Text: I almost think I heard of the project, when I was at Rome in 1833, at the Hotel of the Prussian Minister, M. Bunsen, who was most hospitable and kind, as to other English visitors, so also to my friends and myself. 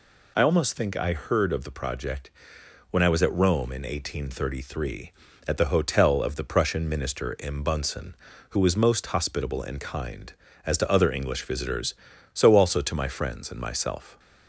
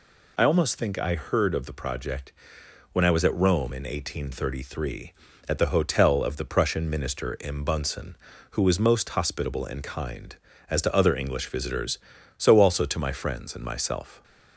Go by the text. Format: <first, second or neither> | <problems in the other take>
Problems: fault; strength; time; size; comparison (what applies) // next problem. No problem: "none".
neither | none